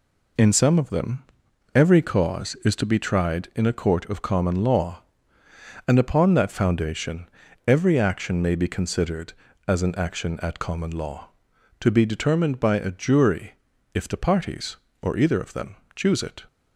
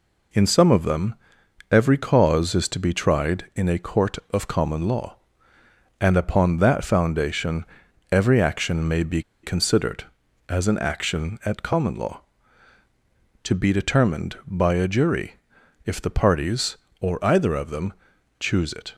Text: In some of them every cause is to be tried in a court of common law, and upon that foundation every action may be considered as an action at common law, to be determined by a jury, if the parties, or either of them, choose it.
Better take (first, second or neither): first